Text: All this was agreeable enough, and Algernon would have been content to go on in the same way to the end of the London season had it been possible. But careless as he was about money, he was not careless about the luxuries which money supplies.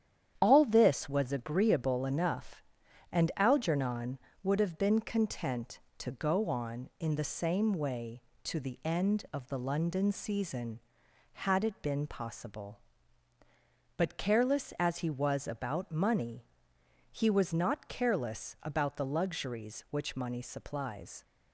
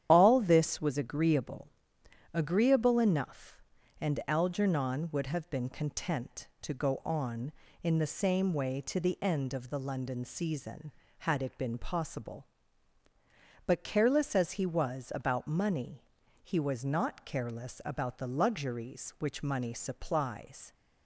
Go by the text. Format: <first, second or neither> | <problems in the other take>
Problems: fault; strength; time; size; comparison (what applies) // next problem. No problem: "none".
first | starts louder than the rest; strong; until 1.1 s; 9.5 dB; strong in the first // says "agreeable" twice; at 2.3 s